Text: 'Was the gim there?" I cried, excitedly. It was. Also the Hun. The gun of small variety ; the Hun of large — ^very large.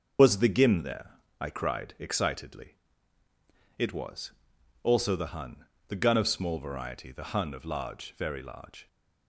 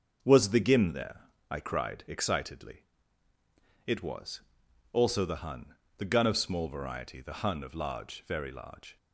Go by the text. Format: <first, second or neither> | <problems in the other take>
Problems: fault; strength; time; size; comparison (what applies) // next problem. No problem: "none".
second | loses the start of "Was"; at 0.1 s; 90 ms // starts louder than the rest; until 1.4 s; 6.5 dB; also in the second